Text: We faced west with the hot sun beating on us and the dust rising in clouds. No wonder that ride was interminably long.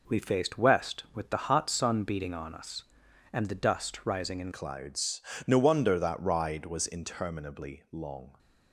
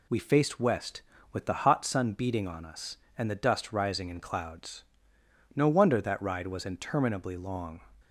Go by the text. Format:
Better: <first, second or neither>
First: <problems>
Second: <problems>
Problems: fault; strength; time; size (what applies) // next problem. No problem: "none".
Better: second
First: changes voice at "clouds"; from 4.5 s on; 3.8 s long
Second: none